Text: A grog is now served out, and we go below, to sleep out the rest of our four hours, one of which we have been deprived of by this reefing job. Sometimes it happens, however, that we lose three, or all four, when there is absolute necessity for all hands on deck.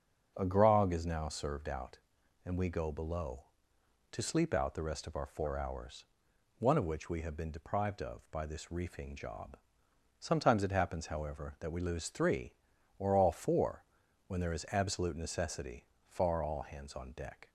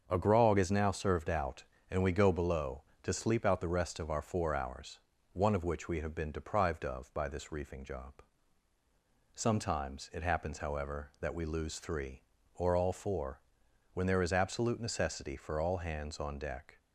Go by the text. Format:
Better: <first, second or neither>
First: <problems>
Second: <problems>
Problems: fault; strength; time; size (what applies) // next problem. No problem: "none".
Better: second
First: starts louder than the rest; until 1.3 s; 6.5 dB // says "far" for "for"; at 16.0 s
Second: starts louder than the rest; until 1.0 s; 7 dB